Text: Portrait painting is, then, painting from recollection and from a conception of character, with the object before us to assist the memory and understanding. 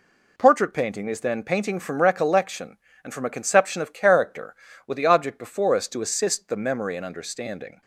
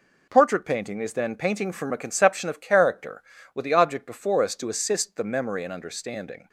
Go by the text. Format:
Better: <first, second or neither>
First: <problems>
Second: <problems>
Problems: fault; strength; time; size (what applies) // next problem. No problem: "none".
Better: first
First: none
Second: skips "recollection and from"; at 1.9 s